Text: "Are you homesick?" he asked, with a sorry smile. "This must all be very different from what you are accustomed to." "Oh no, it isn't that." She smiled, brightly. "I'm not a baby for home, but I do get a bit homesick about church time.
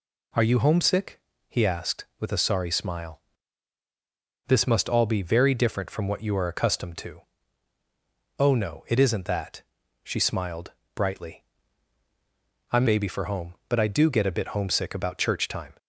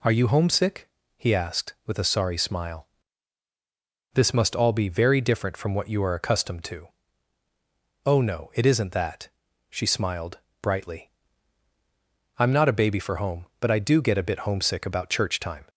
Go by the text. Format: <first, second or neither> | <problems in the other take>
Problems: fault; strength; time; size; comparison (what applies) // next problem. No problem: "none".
second | skips "not a"; at 12.8 s